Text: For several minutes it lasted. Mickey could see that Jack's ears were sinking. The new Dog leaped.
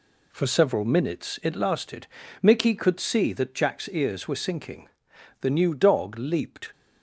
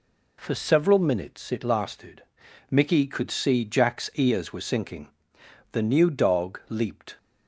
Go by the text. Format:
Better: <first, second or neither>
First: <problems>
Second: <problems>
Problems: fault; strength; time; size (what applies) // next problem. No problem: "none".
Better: first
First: none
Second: skips "that"; at 3.6 s